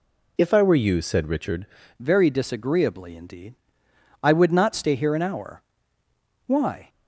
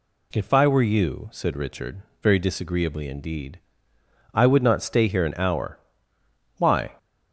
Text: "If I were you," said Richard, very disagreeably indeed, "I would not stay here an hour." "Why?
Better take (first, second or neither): second